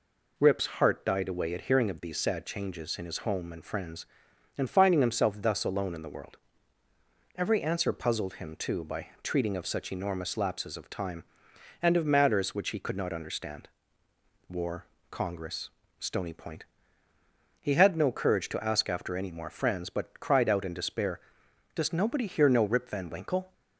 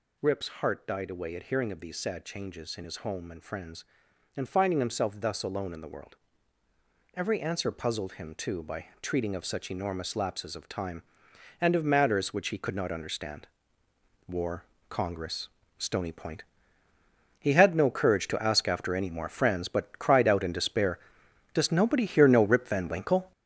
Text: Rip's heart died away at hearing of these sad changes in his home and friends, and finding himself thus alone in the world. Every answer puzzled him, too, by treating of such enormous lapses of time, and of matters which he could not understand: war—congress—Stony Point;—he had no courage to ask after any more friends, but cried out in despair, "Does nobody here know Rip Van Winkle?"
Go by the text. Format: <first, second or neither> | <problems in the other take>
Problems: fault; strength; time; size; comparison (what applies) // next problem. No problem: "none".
first | gets louder; throughout; 7 dB // pauses between "by" and "treating"; slight; at 8.8 s; 0.16 s long; slight in the first